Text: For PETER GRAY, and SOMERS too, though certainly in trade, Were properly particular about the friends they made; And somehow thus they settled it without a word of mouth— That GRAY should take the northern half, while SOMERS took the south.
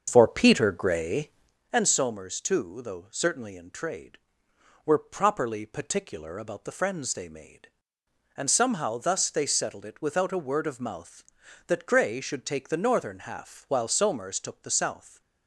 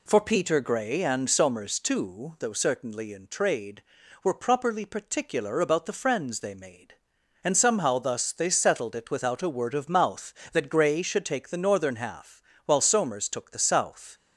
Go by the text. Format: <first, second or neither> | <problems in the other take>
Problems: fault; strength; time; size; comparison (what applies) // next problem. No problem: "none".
second | starts louder than the rest; until 1.7 s; 7 dB